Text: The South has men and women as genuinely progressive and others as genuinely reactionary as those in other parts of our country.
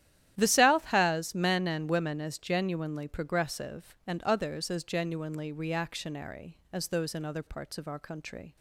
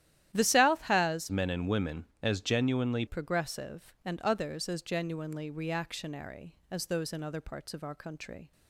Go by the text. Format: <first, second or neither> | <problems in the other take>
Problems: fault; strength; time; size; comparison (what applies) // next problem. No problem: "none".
first | starts louder than the rest; strong; until 1.3 s; 12 dB; strong in the first // changes voice from "men" to "genuinely"; from 1.2 to 3.0 s; 1.8 s long